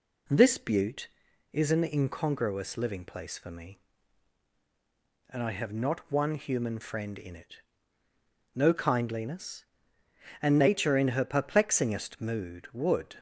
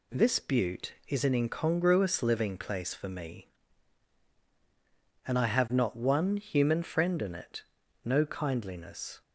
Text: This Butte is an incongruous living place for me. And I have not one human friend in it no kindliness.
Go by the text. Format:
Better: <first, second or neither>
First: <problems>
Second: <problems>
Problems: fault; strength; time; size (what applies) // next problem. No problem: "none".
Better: second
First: pauses between "it" and "no"; noticeable; at 7.5 s; 0.96 s long // goes on to say "And Nature in her perplexingest mood would"; strong; from 10.4 s on; 2.7 s long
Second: pauses between "it" and "no"; at 7.6 s; 0.42 s long